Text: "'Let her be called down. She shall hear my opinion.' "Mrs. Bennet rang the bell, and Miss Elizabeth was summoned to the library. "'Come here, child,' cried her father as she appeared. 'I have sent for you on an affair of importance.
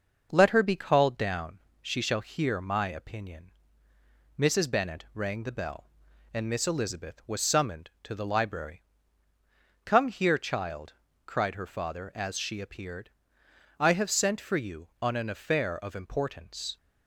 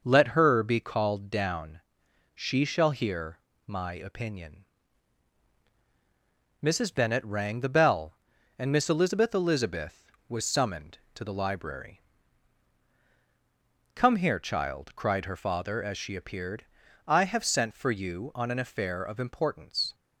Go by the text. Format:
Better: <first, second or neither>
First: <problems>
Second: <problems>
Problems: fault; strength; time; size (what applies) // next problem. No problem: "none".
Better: first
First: none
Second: pauses between "hear" and "my"; slight; at 3.3 s; 0.30 s long // says "Elizabeth" twice; at 9.3 s